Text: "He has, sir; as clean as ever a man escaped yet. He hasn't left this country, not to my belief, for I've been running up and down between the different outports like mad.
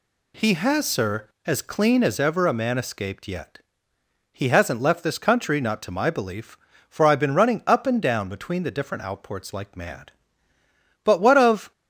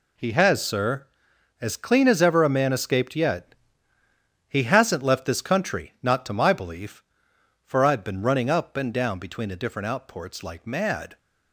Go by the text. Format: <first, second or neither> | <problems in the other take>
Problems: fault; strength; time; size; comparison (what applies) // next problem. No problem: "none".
second | goes on to say "But what of"; noticeable; from 11.0 s on; 0.66 s long